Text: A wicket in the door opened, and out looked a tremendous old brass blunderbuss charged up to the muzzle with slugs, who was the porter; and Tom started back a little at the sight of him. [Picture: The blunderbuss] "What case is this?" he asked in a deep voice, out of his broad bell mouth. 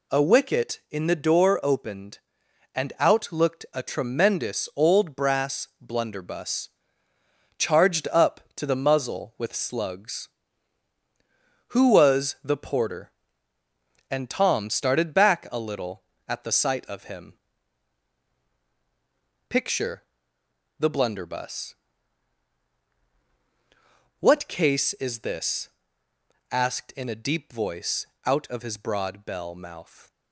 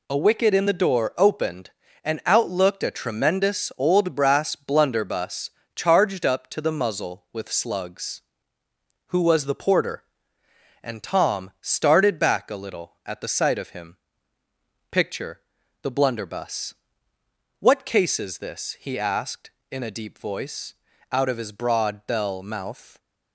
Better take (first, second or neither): second